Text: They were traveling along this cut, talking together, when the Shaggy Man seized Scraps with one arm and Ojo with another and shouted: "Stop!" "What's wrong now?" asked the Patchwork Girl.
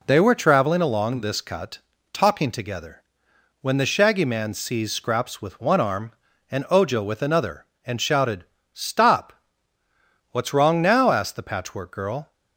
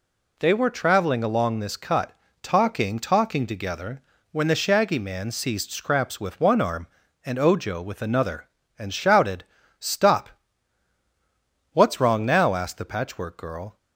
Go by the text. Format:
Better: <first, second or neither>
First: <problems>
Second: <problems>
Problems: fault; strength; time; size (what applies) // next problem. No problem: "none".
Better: first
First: none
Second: says "talking" twice; at 2.9 s